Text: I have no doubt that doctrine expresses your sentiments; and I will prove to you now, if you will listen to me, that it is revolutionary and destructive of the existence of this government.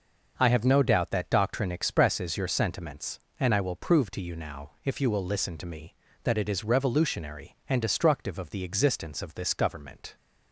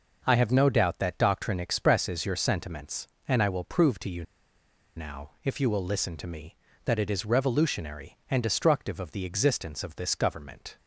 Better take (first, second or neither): first